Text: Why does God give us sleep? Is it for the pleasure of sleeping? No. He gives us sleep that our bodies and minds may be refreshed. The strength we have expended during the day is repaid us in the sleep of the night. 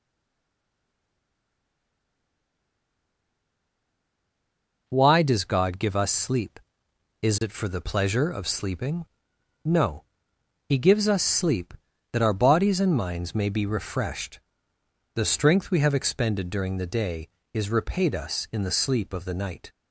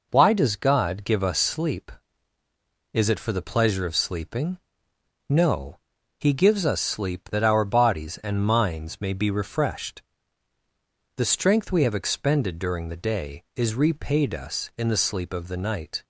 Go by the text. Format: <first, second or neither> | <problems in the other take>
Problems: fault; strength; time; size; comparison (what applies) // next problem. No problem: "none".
second | stays silent before the first word; strong; until 4.8 s; 4.8 s long